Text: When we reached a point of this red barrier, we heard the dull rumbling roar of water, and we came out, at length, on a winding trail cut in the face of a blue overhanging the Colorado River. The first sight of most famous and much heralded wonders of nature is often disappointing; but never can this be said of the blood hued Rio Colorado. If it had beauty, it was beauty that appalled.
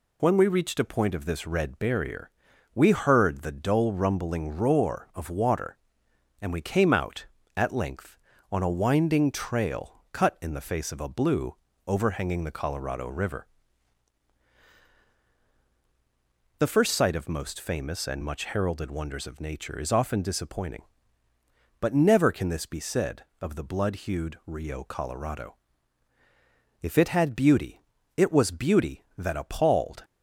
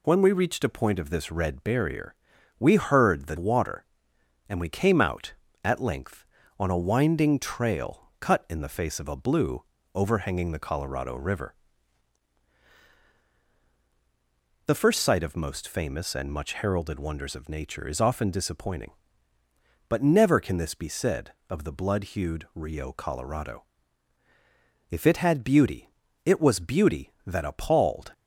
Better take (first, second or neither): first